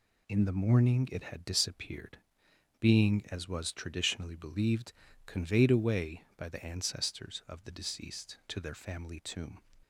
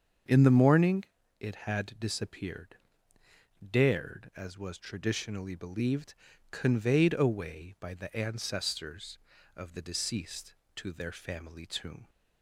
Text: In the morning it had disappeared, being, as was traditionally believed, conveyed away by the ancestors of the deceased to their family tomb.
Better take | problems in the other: first | starts louder than the rest; until 1.6 s; 7 dB // pauses between "morning" and "it"; slight; at 1.0 s; 0.34 s long // says "dared" for "being"; at 3.7 s

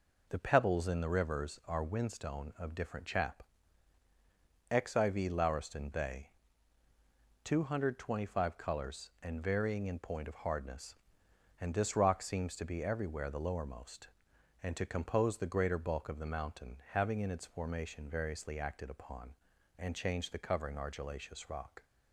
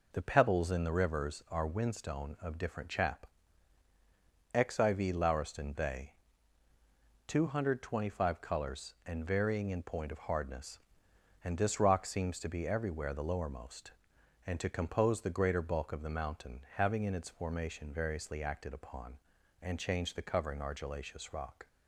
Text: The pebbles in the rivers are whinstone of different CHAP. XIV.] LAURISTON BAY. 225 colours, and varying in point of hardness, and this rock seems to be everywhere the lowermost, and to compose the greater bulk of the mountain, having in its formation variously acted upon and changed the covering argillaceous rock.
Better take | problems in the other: neither | none

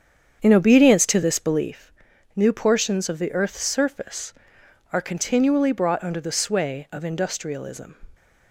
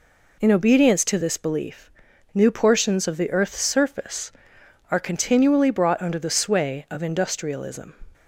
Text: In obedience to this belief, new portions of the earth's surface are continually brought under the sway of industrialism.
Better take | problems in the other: second | starts louder than the rest; strong; until 1.7 s; 8 dB

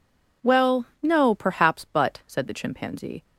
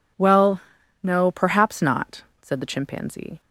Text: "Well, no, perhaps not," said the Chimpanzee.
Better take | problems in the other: second | says "but" for "not"; at 1.8 s

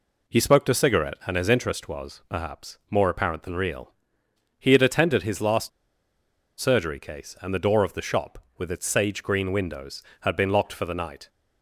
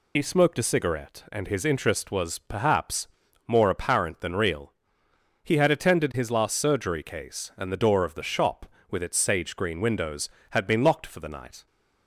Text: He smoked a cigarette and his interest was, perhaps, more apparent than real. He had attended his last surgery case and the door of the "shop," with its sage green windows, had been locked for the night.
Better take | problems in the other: second | pauses between "last" and "surgery"; noticeable; at 5.6 s; 0.90 s long

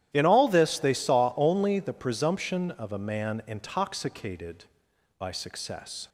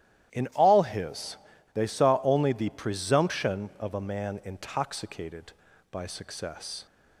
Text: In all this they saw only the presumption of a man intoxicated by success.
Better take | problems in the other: first | starts louder than the rest; strong; until 1.7 s; 12.5 dB; strong in the first // says "his" for "this"; at 0.8 s

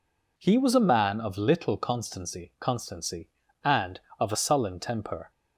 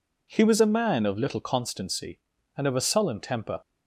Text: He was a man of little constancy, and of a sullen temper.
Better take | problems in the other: second | says "constancy" twice; at 2.5 s

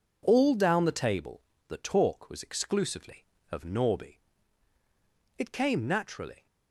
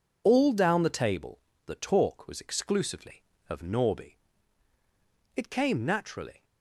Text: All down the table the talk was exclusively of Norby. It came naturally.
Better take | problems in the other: first | loses the start of "All"; at 0.2 s; 35 ms // pauses between "table" and "the"; slight; at 1.3 s; 0.26 s long; slight in the first

